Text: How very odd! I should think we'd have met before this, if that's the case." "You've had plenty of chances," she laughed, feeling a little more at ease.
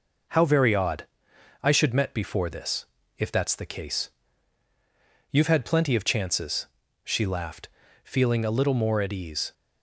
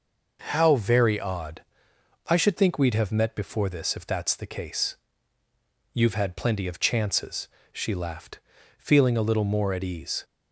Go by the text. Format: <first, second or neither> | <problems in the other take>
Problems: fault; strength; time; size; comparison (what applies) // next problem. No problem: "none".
second | skips "think we'd have"; at 1.9 s